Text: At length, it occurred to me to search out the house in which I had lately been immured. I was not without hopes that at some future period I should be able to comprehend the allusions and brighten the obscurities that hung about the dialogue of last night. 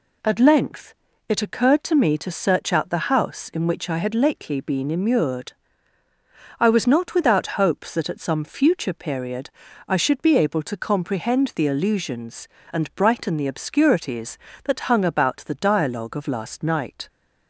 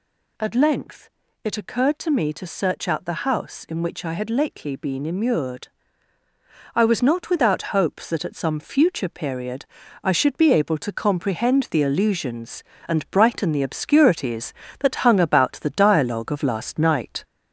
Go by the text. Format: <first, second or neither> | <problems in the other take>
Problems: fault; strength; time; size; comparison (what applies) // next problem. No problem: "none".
first | gets louder; throughout; 3.5 dB // pauses between "period" and "I"; at 9.6 s; 0.40 s long; also in the first